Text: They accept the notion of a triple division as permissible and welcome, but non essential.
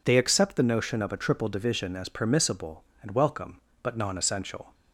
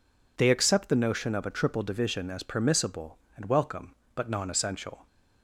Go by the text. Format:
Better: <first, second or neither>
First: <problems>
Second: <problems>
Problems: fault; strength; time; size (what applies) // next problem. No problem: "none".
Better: neither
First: none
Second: none